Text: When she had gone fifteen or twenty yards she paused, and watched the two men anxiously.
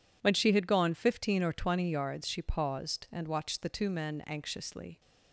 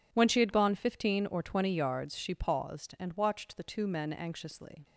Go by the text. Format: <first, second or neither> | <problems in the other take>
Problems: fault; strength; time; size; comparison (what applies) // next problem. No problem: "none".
neither | none